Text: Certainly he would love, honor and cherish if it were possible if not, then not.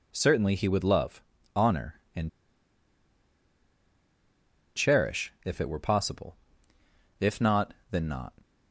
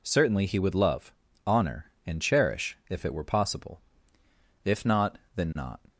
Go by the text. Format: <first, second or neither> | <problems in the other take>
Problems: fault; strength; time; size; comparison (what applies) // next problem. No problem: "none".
second | pauses between "and" and "cherish"; strong; at 2.2 s; 2.4 s long // pauses between "possible" and "if"; noticeable; at 6.3 s; 0.84 s long; noticeable in the second